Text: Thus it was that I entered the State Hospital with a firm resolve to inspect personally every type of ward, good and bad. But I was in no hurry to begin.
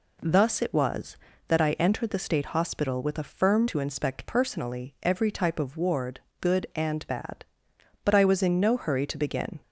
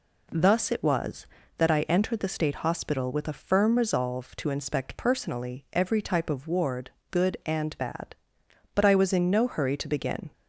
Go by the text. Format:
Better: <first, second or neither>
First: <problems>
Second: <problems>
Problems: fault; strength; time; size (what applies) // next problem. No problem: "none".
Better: second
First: skips "resolve"; at 3.6 s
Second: none